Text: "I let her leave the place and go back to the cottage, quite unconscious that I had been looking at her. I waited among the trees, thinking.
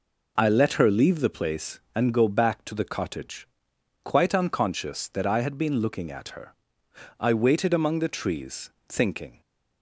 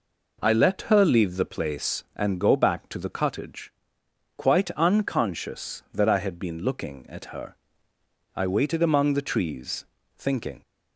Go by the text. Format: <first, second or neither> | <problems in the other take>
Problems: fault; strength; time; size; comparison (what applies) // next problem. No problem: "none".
neither | none